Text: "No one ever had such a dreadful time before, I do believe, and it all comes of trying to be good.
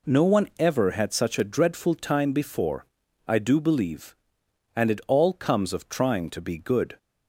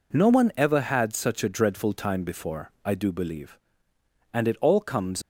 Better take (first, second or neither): first